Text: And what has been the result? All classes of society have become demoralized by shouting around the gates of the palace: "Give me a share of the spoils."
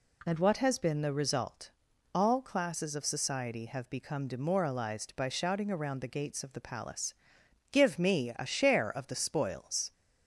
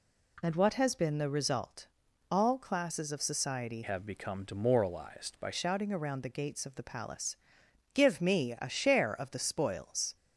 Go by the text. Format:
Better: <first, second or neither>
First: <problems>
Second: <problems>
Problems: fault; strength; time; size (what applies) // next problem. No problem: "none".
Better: first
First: none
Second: changes voice from "have" to "by"; from 3.8 to 5.4 s; 1.6 s long